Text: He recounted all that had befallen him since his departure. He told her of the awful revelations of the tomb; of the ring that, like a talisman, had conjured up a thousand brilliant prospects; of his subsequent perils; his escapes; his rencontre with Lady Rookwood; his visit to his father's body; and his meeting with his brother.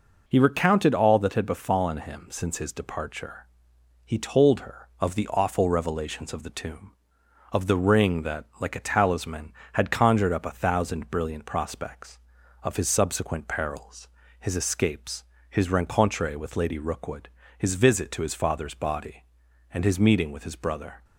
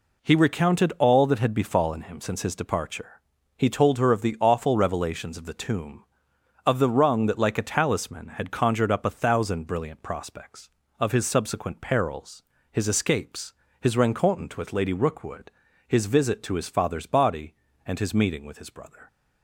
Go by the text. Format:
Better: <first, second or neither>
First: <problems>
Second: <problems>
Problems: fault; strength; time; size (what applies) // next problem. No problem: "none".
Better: first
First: none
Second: says "rung" for "ring"; at 6.8 s